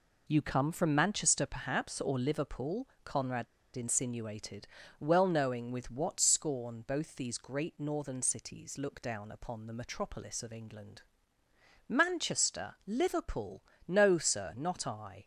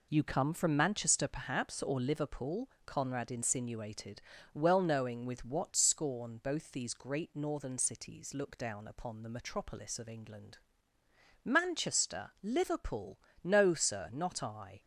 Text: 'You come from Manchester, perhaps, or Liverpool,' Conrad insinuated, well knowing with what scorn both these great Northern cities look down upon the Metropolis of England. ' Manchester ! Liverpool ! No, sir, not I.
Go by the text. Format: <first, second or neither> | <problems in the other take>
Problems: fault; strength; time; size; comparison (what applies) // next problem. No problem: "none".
second | pauses between "Conrad" and "insinuated"; slight; at 3.4 s; 0.29 s long